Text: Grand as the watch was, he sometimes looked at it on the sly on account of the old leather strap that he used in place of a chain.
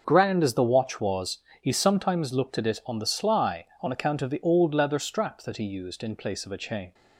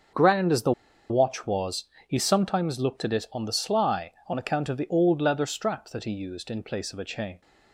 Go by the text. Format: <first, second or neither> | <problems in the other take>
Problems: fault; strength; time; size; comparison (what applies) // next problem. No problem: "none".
first | starts louder than the rest; until 1.5 s; 6.5 dB; also in the first // pauses between "the" and "watch"; at 0.7 s; 0.38 s long